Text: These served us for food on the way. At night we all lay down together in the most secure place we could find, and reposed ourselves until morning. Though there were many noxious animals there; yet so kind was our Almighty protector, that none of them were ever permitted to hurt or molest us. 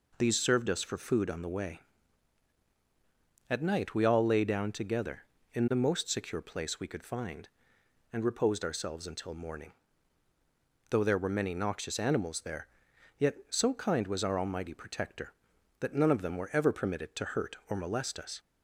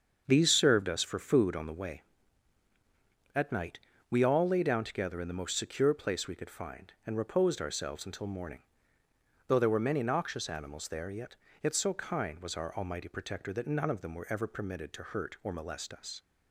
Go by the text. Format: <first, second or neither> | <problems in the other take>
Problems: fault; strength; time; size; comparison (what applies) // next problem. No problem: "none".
first | starts louder than the rest; until 1.2 s; 7 dB // pauses between "night" and "we"; slight; at 3.7 s; 0.30 s long // says "yet" twice; at 11.6 s